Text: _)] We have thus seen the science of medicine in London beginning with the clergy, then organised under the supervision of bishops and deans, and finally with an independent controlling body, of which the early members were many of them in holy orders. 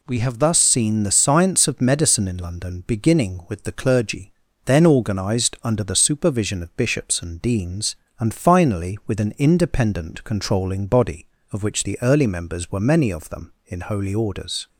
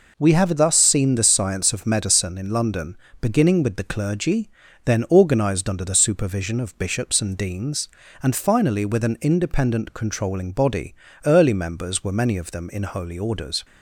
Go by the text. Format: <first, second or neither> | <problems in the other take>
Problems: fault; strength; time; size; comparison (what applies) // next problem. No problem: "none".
first | pauses between "London" and "beginning"; slight; at 2.9 s; 0.24 s long // skips "of which the"; at 11.1 s